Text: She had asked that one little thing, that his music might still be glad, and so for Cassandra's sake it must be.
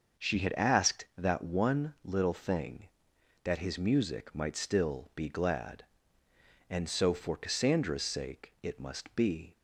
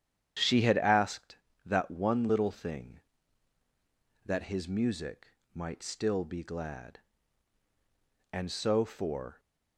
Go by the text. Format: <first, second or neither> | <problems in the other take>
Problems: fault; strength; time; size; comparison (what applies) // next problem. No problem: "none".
first | starts louder than the rest; strong; until 1.7 s; 9 dB // pauses between "music" and "might"; slight; at 5.2 s; 0.24 s long // stops before "Cassandra's sake it must be"; at 9.3 s